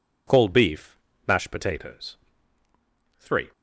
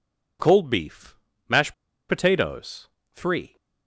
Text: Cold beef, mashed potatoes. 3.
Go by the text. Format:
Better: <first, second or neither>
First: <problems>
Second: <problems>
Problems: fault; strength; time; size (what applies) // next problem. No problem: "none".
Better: first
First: none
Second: pauses between "mashed" and "potatoes"; slight; at 1.7 s; 0.35 s long